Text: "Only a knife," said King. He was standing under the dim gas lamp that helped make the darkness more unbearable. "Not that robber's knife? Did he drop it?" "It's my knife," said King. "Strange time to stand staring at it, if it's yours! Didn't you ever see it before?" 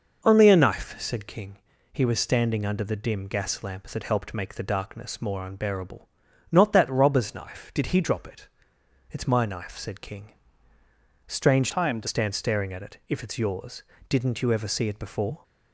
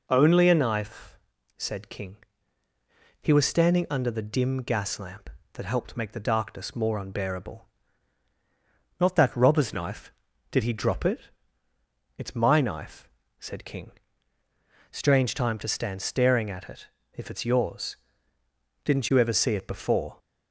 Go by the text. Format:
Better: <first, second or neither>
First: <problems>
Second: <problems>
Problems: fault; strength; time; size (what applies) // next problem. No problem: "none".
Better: second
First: changes voice from "time" to "to"; from 11.7 to 12.0 s; 0.3 s long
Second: none